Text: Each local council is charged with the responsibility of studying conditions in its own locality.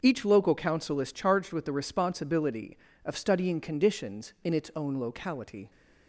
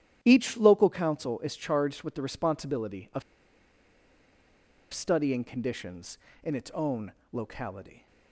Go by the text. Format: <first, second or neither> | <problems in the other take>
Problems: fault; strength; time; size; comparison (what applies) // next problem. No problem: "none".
first | starts louder than the rest; strong; until 1.2 s; 10 dB; also in the first // pauses between "of" and "studying"; strong; at 3.2 s; 1.7 s long // pauses between "own" and "locality"; slight; at 7.1 s; 0.20 s long